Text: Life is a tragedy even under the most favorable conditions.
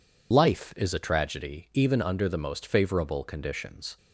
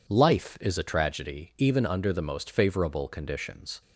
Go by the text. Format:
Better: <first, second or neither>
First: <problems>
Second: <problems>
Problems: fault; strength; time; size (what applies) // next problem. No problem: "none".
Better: second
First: loses the start of "Life"; at 0.3 s; 60 ms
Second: none